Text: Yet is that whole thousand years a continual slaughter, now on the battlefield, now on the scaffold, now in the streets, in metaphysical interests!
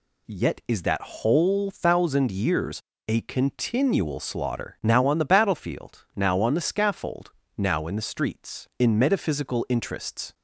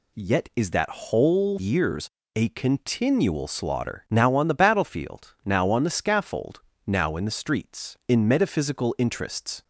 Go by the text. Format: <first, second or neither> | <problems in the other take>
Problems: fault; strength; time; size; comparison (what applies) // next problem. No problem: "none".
first | skips "thousand"; at 1.5 s // pauses between "years" and "a"; slight; at 2.0 s; 0.28 s long; slight in the first